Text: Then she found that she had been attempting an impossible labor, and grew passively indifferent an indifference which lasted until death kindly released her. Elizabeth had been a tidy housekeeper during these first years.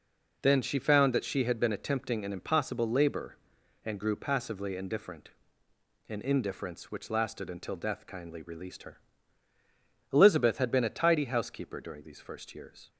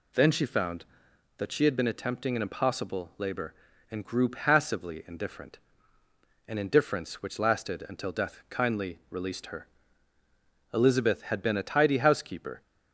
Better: first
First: pauses between "indifferent" and "an"; noticeable; at 5.2 s; 0.80 s long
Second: pauses between "indifferent" and "an"; noticeable; at 5.5 s; 0.88 s long // stops before "during these first years"; at 12.6 s

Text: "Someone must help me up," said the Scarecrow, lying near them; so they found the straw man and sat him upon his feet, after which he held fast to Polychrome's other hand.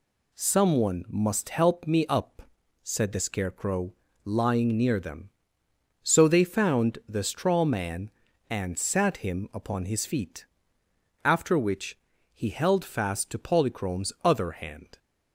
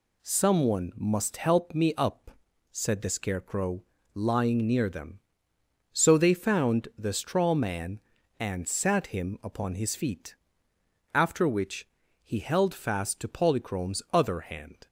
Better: neither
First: pauses between "which" and "he"; slight; at 11.9 s; 0.34 s long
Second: pauses between "which" and "he"; slight; at 11.8 s; 0.34 s long

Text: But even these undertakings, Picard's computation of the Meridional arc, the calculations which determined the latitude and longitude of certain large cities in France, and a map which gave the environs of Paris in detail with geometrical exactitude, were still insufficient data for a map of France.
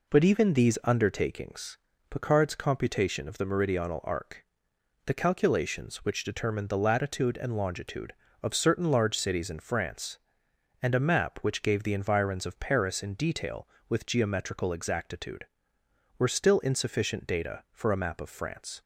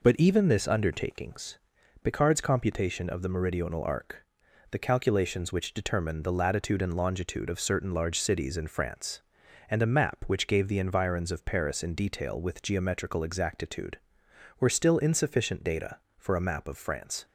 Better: first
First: none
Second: says "this" for "these"; at 0.4 s

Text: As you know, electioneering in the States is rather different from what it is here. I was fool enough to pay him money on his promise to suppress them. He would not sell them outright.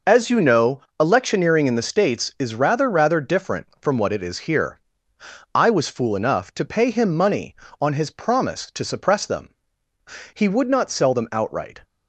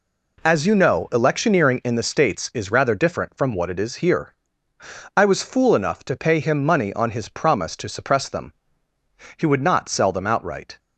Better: second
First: says "rather" twice; at 2.8 s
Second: none

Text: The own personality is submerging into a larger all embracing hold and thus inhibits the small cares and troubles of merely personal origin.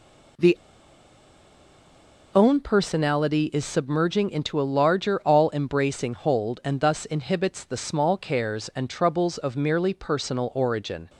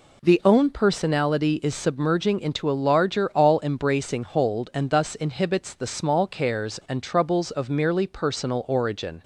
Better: second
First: pauses between "The" and "own"; strong; at 0.5 s; 1.7 s long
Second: none

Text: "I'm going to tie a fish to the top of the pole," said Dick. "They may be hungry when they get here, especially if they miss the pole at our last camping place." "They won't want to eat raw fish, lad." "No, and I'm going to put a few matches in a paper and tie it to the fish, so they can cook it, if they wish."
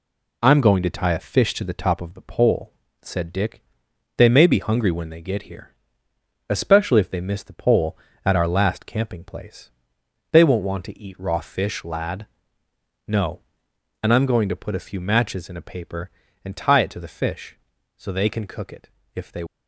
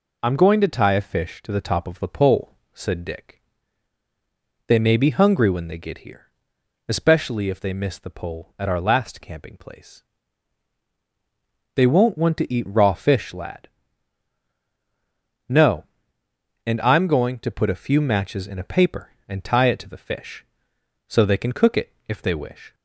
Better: second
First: stops before "wish"; at 19.4 s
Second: none

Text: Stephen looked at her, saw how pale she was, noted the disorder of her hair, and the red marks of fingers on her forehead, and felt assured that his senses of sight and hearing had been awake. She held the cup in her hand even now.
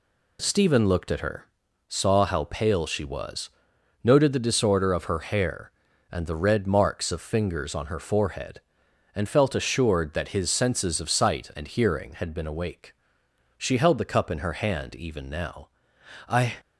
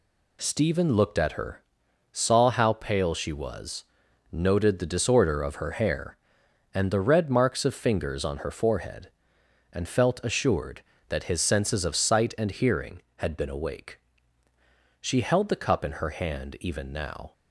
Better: second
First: goes on to say "I"; slight; from 16.2 s on; 0.24 s long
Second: none

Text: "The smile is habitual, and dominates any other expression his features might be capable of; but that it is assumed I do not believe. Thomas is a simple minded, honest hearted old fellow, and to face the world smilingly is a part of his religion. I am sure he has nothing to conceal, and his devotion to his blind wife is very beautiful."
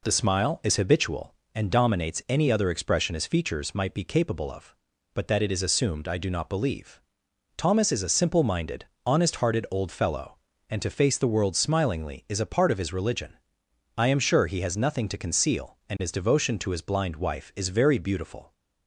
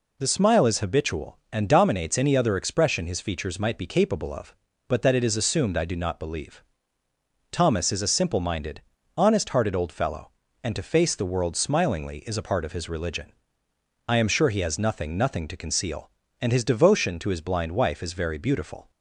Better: first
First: none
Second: says "nothing" twice; at 15.1 s

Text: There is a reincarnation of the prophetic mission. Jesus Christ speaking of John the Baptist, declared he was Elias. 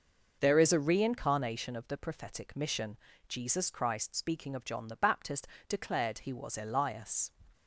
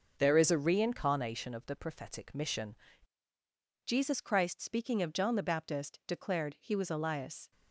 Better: first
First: none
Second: changes voice at "Jesus"; from 3.8 s on; 3.7 s long

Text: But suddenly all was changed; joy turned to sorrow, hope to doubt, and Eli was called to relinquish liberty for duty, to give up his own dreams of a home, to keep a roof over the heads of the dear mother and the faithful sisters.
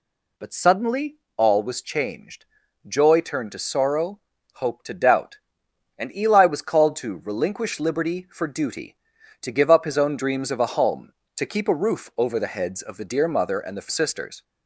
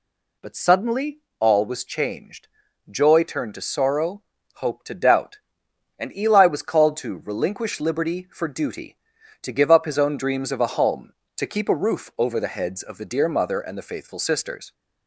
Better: second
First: pauses between "suddenly" and "all"; slight; at 1.1 s; 0.20 s long // skips "faithful"; at 13.8 s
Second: pauses between "suddenly" and "all"; slight; at 1.1 s; 0.20 s long

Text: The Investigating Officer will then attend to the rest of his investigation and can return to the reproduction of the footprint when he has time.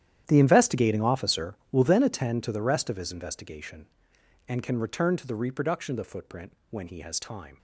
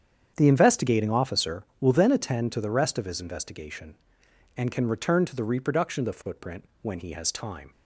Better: second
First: gets quieter; strong; throughout; 15.5 dB // starts louder than the rest; strong; until 1.2 s; 10.5 dB // pauses between "footprint" and "when"; slight; at 6.5 s; 0.20 s long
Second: starts louder than the rest; strong; until 1.3 s; 8 dB // pauses between "footprint" and "when"; slight; at 6.6 s; 0.20 s long

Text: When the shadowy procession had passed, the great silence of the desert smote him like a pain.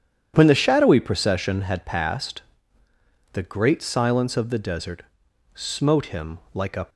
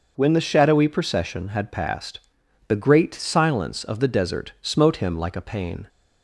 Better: second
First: pauses between "desert" and "smote"; noticeable; at 5.0 s; 0.76 s long // stops before "pain"; at 6.8 s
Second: none

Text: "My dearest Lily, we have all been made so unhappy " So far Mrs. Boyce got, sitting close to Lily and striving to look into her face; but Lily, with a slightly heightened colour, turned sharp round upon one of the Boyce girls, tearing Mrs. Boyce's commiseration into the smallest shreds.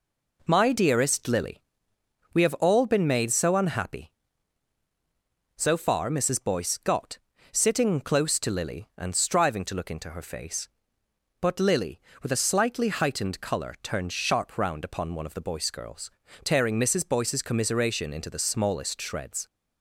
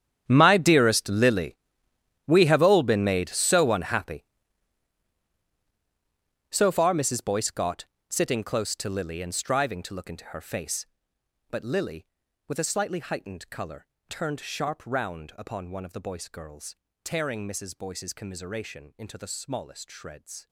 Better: first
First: none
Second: gets quieter; strong; throughout; 9 dB

